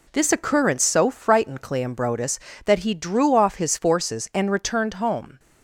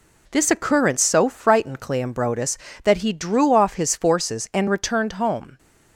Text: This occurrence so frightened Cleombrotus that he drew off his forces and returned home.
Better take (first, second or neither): neither